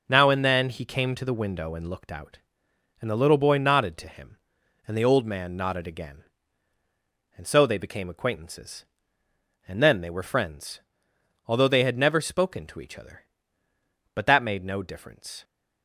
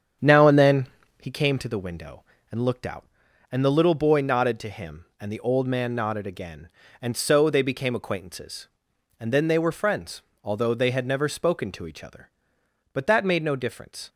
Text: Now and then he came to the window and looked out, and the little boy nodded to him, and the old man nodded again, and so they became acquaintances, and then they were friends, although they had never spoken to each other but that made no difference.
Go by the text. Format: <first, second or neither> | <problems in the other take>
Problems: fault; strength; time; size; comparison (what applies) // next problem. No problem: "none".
first | starts louder than the rest; strong; until 1.3 s; 8 dB // pauses between "then" and "he"; slight; at 0.8 s; 0.34 s long